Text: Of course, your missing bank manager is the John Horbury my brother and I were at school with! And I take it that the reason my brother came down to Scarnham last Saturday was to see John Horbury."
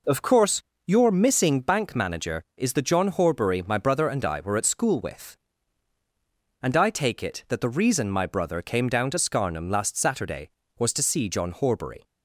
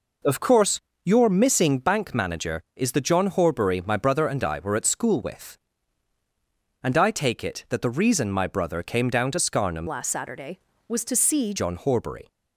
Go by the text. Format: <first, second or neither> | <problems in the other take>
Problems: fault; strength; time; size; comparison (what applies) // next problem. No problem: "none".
first | changes voice from "last" to "see"; from 9.8 to 11.5 s; 1.7 s long